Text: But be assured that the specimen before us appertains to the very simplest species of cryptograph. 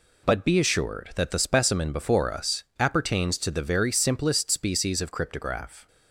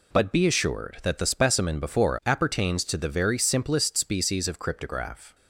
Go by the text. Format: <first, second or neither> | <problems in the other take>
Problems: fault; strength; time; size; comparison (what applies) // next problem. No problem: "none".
first | skips "us"; at 2.2 s